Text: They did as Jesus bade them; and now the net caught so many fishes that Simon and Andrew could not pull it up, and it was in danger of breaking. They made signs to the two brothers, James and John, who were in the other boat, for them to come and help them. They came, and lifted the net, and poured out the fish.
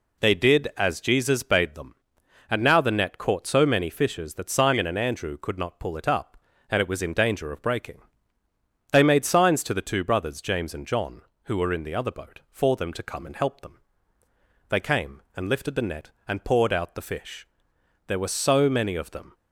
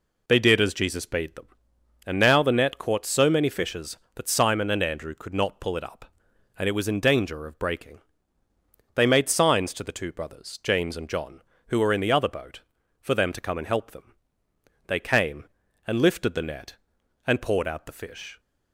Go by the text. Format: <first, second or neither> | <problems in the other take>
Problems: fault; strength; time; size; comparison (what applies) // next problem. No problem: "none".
second | goes on to say "There were so many of them"; noticeable; from 18.0 s on; 1.2 s long